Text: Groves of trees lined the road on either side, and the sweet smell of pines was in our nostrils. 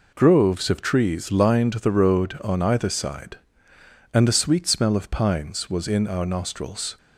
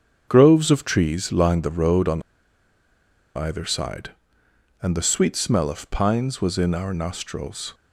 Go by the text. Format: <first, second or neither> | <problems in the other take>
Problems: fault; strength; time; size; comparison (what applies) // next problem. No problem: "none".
first | starts louder than the rest; strong; until 1.2 s; 7.5 dB // pauses between "on" and "either"; at 2.2 s; 1.1 s long